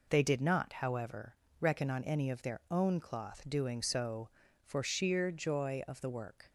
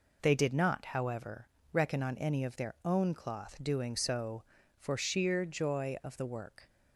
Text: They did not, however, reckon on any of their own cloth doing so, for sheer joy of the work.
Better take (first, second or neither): neither